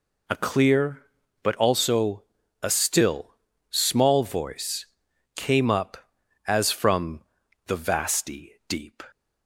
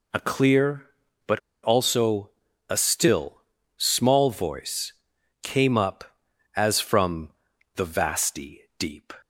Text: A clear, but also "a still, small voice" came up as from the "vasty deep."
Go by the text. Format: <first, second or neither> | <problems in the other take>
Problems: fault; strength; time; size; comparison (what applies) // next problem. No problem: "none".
first | pauses between "but" and "also"; slight; at 1.3 s; 0.24 s long // pauses between "also" and "a"; slight; at 2.3 s; 0.36 s long; slight in the first // pauses between "voice" and "came"; noticeable; at 4.9 s; 0.52 s long; noticeable in the first // pauses between "from" and "the"; noticeable; at 7.2 s; 0.46 s long; noticeable in the first // pauses between "vasty" and "deep"; slight; at 8.6 s; 0.18 s long; slight in the first